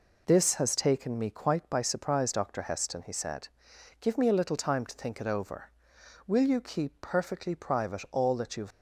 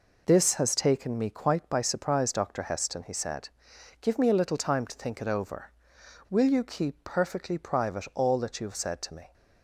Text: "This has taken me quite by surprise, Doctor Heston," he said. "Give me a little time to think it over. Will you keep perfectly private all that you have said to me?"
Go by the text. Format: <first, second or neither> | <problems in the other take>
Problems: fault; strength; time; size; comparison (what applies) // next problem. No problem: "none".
second | stops before "said to me"; at 8.7 s